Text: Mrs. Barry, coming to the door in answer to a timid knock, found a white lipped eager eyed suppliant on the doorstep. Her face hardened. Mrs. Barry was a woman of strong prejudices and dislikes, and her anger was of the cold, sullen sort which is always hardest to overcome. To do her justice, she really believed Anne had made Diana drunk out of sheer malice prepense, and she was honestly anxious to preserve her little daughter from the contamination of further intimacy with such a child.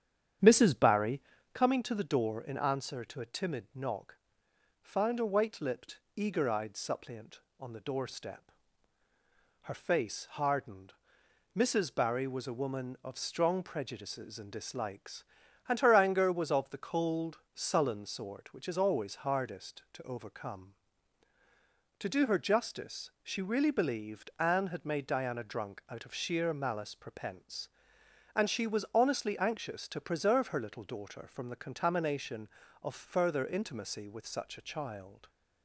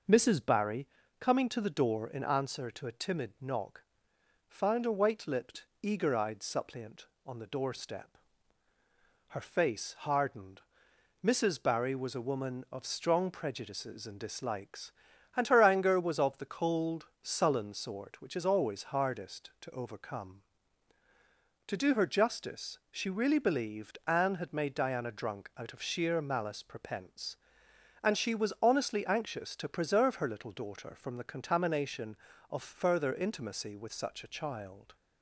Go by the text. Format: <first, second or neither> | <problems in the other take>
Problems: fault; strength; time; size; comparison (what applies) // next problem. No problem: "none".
second | starts louder than the rest; strong; until 1.7 s; 9 dB // pauses between "lipped" and "eager"; slight; at 5.9 s; 0.20 s long; slight in the second